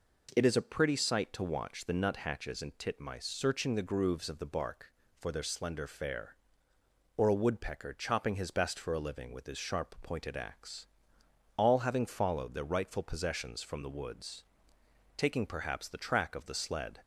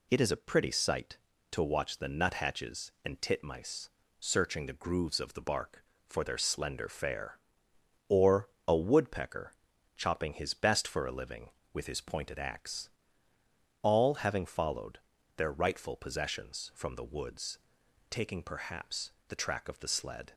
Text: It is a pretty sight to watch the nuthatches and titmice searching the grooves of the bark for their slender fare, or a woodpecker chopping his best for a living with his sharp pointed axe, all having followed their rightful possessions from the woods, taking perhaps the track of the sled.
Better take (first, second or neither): first